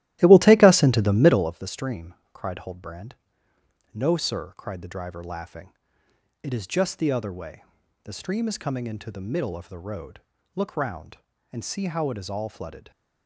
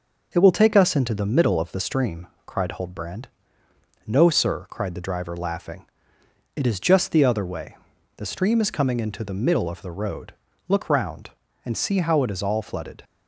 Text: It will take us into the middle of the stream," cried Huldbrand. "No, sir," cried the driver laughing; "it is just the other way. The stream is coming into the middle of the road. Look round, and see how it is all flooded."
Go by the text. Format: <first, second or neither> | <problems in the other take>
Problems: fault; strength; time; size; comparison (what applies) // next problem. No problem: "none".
second | starts louder than the rest; strong; until 1.5 s; 15 dB